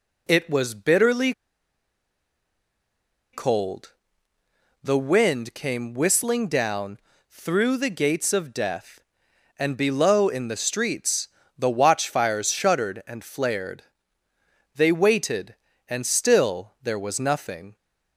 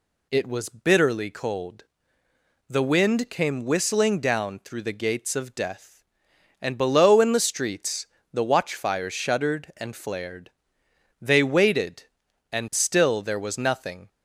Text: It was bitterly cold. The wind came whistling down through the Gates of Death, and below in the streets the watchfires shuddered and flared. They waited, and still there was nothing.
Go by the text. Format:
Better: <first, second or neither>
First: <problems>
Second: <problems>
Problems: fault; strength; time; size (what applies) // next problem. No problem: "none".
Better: second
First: pauses between "bitterly" and "cold"; strong; at 1.3 s; 2.0 s long // pauses between "down" and "through"; slight; at 6.9 s; 0.32 s long // pauses between "streets" and "the"; slight; at 11.2 s; 0.28 s long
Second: pauses between "streets" and "the"; slight; at 8.0 s; 0.26 s long